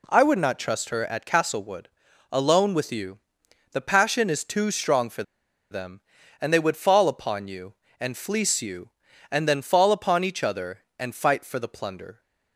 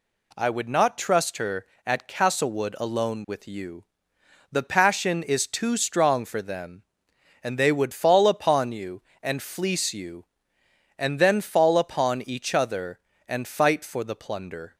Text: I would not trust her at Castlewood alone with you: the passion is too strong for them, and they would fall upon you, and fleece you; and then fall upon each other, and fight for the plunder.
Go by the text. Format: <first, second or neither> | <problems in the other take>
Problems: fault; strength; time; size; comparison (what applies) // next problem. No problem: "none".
second | pauses between "Castlewood" and "alone"; at 1.8 s; 0.42 s long // pauses between "for" and "them"; noticeable; at 5.2 s; 0.48 s long